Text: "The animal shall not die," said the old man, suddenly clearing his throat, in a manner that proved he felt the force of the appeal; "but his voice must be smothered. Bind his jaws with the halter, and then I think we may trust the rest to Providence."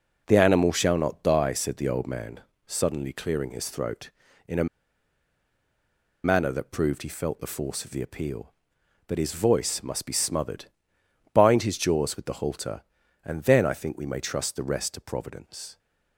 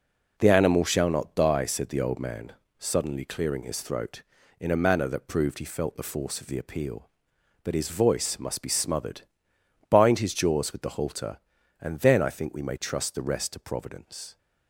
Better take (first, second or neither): second